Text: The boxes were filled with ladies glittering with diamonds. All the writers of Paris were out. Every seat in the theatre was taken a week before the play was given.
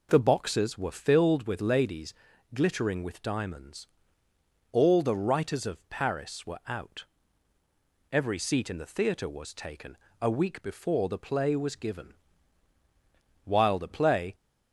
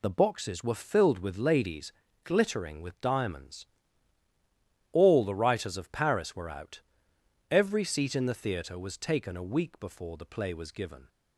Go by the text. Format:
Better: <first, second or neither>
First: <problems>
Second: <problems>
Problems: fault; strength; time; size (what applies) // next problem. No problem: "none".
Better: second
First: pauses between "ladies" and "glittering"; at 2.1 s; 0.40 s long // pauses between "taken" and "a"; slight; at 9.9 s; 0.20 s long // goes on to say "While the play"; noticeable; from 13.4 s on; 0.90 s long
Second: pauses between "ladies" and "glittering"; slight; at 1.9 s; 0.32 s long